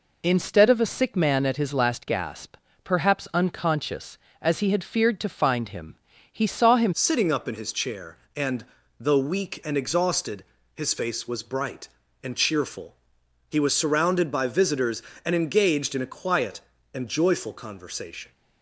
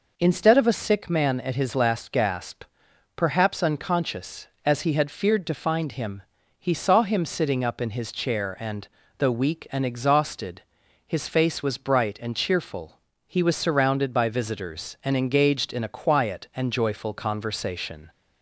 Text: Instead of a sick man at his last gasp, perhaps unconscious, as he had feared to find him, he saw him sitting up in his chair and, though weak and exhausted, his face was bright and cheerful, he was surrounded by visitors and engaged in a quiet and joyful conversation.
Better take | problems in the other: second | changes voice at "sitting"; from 6.9 s on; 11.4 s long

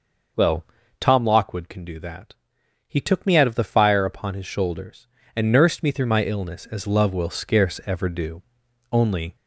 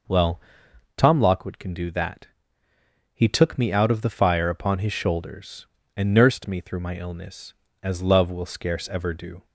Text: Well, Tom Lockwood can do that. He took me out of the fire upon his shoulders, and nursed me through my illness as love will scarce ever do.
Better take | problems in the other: second | goes on to say "Only"; slight; from 8.9 s on; 0.44 s long

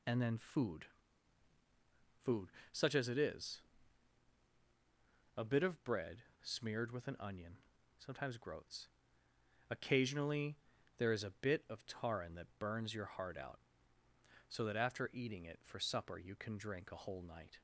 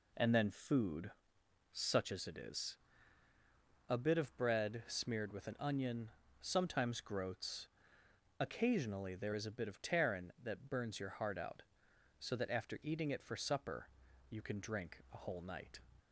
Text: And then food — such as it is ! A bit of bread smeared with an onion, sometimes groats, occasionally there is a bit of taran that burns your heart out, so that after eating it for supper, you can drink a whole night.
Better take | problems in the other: second | says "food" twice; at 2.2 s // pauses between "bread" and "smeared"; slight; at 6.2 s; 0.21 s long // pauses between "occasionally" and "there"; at 10.5 s; 0.40 s long

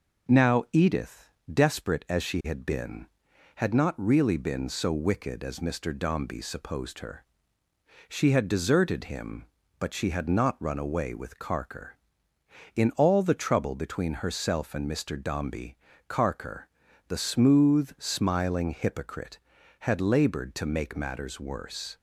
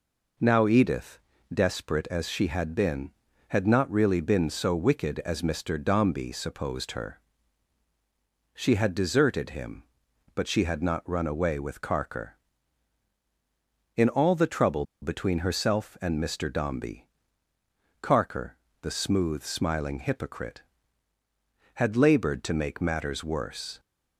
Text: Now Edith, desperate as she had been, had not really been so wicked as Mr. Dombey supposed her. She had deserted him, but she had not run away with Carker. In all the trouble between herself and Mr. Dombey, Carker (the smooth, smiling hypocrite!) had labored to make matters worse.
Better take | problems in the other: first | pauses between "trouble" and "between"; slight; at 14.8 s; 0.18 s long

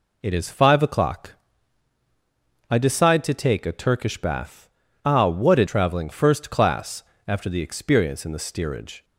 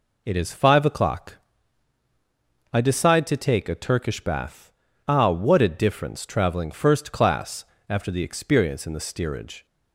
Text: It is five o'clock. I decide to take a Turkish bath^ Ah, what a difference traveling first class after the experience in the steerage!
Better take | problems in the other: second | pauses between "bath" and "Ah"; slight; at 4.6 s; 0.36 s long; slight in the second // skips "difference"; at 5.6 s // pauses between "class" and "after"; slight; at 7.0 s; 0.24 s long; slight in the second

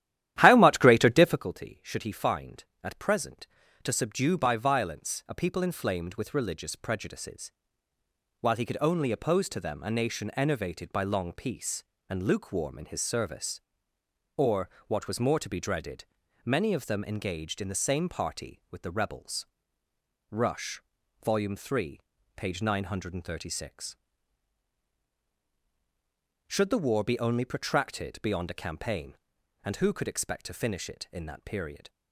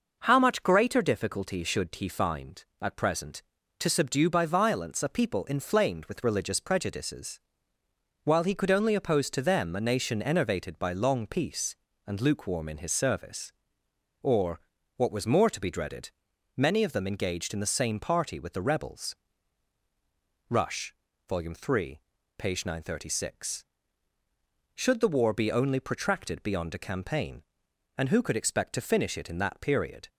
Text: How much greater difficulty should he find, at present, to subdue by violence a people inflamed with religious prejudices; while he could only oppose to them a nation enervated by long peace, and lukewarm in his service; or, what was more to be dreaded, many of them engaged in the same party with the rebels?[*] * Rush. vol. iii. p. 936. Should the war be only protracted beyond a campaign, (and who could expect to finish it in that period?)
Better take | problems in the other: second | starts louder than the rest; strong; until 1.5 s; 12.5 dB

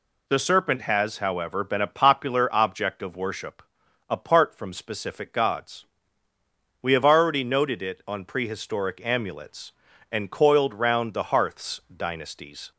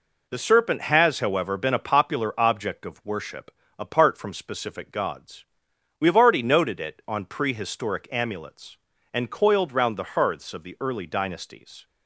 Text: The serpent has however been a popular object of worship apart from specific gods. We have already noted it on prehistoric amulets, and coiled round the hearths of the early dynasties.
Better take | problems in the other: second | pauses between "worship" and "apart"; noticeable; at 3.6 s; 0.48 s long; slight in the second // skips "of the early"; at 11.8 s

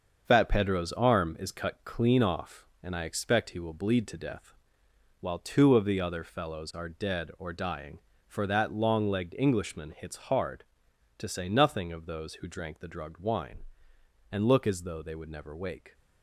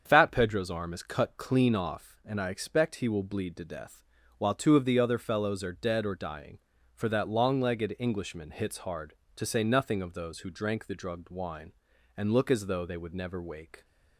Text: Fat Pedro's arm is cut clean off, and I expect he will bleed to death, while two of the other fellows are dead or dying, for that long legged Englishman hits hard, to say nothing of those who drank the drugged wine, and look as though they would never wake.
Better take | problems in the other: second | gets quieter; strong; throughout; 7 dB // starts louder than the rest; until 1.2 s; 6.5 dB; strong in the second

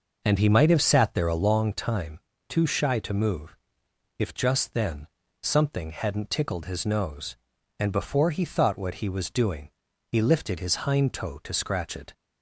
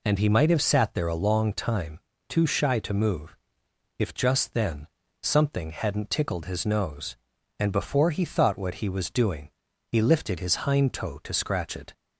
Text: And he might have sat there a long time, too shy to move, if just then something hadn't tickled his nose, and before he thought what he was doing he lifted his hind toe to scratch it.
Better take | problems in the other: second | starts louder than the rest; noticeable; until 1.6 s; 5.5 dB // pauses between "then" and "something"; slight; at 5.0 s; 0.34 s long; slight in the second // pauses between "doing" and "he"; at 9.7 s; 0.38 s long; also in the second

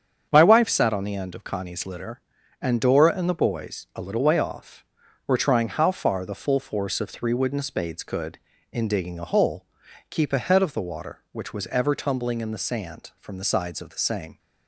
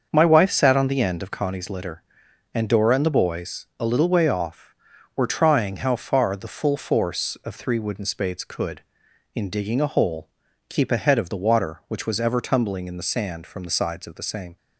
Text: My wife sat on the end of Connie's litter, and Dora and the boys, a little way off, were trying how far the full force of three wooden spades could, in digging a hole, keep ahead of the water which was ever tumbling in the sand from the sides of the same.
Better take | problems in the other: neither | starts louder than the rest; the same in both

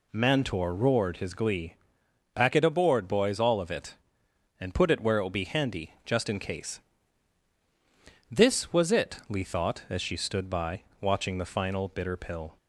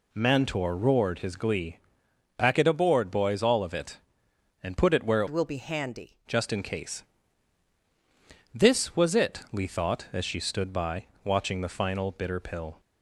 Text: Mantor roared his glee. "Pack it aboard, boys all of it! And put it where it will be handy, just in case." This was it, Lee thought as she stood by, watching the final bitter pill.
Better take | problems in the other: first | changes voice from "will" to "handy"; from 5.2 to 6.1 s; 0.9 s long

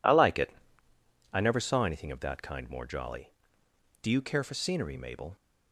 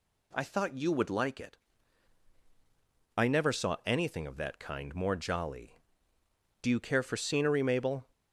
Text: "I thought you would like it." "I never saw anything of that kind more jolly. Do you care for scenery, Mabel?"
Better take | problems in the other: second | skips "thought you would"; at 0.1 s

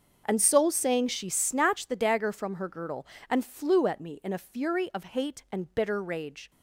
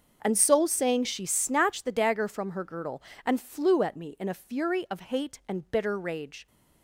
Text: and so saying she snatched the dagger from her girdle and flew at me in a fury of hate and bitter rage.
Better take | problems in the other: neither | starts louder than the rest; the same in both

